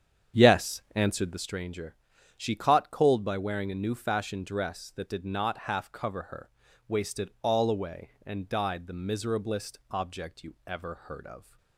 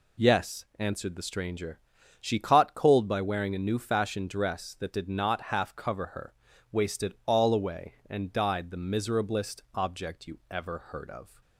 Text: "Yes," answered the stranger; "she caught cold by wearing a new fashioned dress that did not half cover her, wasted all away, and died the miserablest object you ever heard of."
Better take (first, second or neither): second